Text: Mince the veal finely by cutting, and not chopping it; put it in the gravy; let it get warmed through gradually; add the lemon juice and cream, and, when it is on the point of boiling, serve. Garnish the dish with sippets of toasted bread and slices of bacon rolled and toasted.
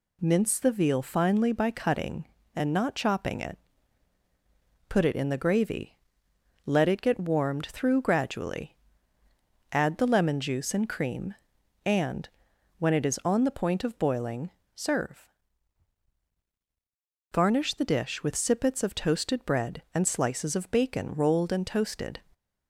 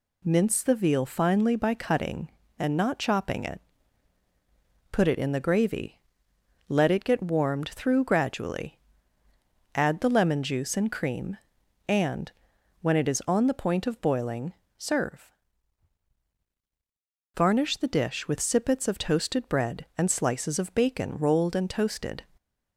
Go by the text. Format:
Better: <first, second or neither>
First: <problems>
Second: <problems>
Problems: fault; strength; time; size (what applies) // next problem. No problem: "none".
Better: neither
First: none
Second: none